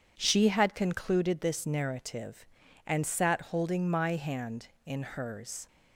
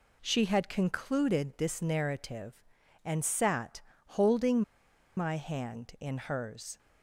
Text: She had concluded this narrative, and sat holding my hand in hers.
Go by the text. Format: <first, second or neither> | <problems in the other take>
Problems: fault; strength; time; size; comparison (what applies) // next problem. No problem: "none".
first | pauses between "sat" and "holding"; slight; at 3.7 s; 0.26 s long // pauses between "holding" and "my"; noticeable; at 4.6 s; 0.55 s long